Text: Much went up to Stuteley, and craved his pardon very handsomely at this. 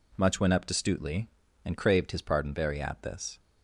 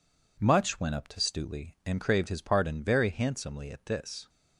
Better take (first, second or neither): second